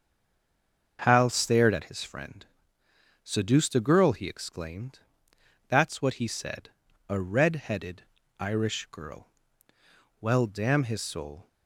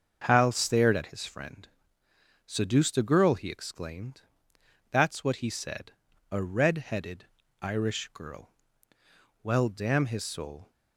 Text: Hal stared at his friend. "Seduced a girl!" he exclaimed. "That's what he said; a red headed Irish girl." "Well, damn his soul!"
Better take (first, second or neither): second